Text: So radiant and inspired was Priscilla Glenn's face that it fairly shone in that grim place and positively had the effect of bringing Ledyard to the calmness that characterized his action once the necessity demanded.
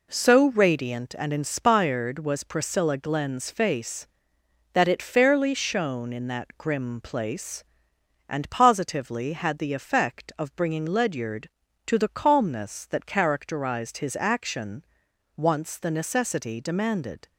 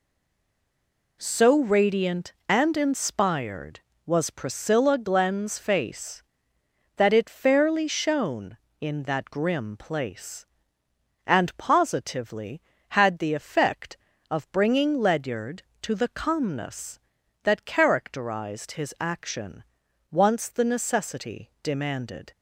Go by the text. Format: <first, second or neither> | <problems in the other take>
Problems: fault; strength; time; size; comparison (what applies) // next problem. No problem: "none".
first | stays silent before the first word; noticeable; until 1.2 s; 1.2 s long // pauses between "action" and "once"; noticeable; at 19.6 s; 0.46 s long; noticeable in the first